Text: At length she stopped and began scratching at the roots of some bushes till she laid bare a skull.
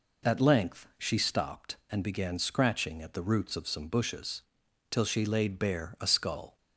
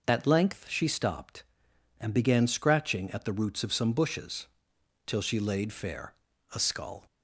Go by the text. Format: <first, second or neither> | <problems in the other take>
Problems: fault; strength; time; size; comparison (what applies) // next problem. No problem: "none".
first | pauses between "bushes" and "till"; noticeable; at 4.4 s; 0.59 s long; noticeable in the first // says "fair" for "bare"; at 5.7 s